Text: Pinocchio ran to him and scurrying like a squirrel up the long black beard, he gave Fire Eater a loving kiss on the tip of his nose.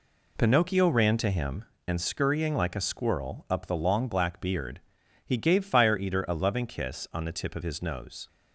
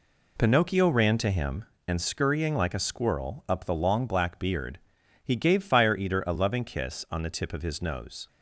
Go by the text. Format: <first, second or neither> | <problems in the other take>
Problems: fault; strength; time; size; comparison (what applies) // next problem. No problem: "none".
neither | none